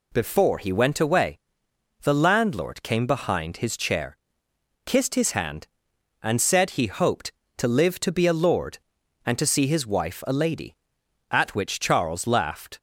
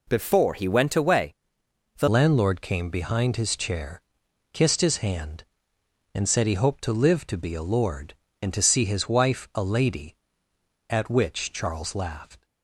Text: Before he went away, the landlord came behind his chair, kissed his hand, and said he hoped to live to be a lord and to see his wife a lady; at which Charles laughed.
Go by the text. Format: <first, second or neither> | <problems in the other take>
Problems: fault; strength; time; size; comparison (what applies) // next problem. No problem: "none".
first | changes voice at "landlord"; from 2.0 s on; 10.4 s long